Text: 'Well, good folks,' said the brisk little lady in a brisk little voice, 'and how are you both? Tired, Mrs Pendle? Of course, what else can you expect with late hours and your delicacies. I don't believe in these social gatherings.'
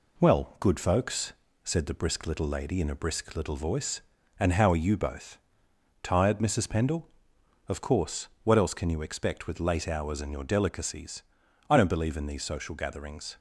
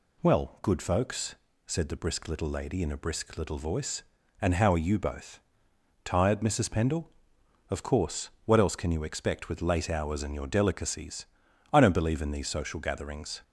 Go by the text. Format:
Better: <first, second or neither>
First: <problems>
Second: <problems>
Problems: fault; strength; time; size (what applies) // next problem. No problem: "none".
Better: second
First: gets quieter; slight; throughout; 3 dB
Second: none